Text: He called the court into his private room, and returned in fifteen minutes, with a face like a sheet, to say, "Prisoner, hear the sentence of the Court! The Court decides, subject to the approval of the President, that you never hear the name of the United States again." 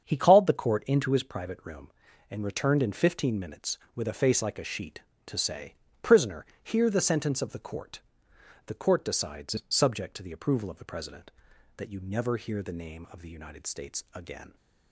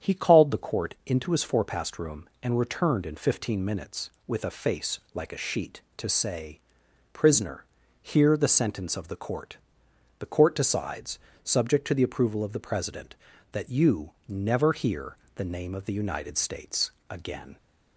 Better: first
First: starts louder than the rest; strong; until 1.0 s; 7.5 dB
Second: starts louder than the rest; strong; until 1.1 s; 8 dB // says "forepast" for "private"; at 1.4 s // pauses between "hear" and "the"; slight; at 15.1 s; 0.18 s long // pauses between "States" and "again"; slight; at 16.9 s; 0.20 s long

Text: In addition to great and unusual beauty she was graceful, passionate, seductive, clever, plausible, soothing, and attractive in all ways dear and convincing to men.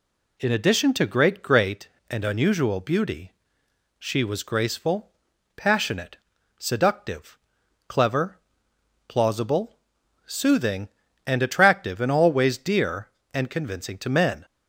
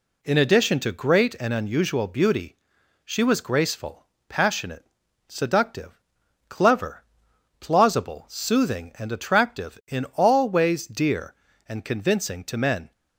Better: second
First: says "great" twice; at 1.4 s // pauses between "beauty" and "she"; noticeable; at 3.3 s; 0.68 s long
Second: pauses between "beauty" and "she"; noticeable; at 2.5 s; 0.48 s long

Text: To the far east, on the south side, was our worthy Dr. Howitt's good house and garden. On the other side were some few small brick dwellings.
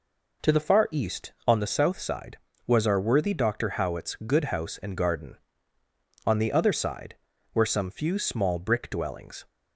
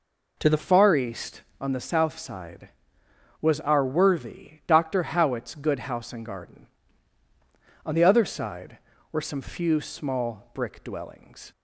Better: first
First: none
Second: changes voice at "far"; from 0.5 s on; 11.0 s long

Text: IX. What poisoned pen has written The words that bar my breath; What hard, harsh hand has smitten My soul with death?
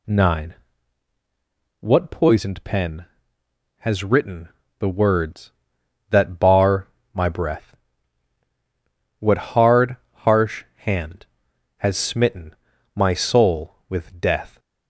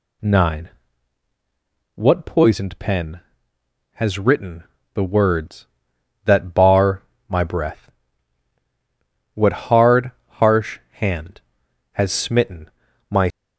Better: first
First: pauses between "written" and "The"; slight; at 4.4 s; 0.30 s long // pauses between "bar" and "my"; slight; at 6.8 s; 0.26 s long // pauses between "smitten" and "My"; at 12.5 s; 0.40 s long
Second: pauses between "written" and "The"; slight; at 4.6 s; 0.30 s long // pauses between "bar" and "my"; slight; at 7.0 s; 0.26 s long // pauses between "smitten" and "My"; at 12.6 s; 0.40 s long // stops before "soul with death"; at 13.2 s

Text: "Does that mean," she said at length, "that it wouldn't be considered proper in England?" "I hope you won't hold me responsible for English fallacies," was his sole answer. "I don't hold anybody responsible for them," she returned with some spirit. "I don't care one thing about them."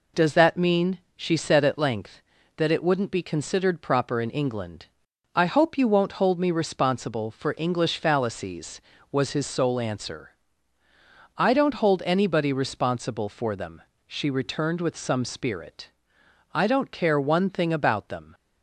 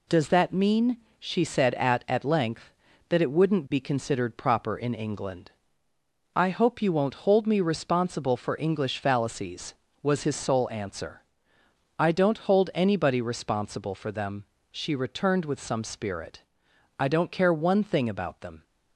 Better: first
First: none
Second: says "at" twice; at 2.0 s

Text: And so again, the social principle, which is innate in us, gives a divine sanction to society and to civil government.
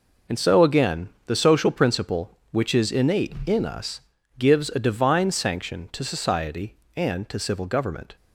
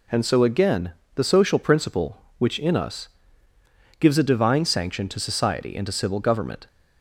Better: first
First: none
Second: skips "is innate"; at 2.5 s

